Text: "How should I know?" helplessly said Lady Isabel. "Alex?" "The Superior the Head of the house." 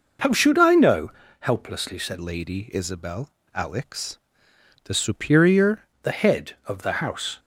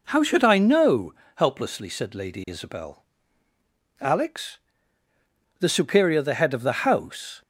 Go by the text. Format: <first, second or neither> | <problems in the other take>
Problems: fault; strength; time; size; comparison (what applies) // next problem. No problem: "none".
second | changes voice from "Lady" to "Superior"; from 2.2 to 5.8 s; 3.6 s long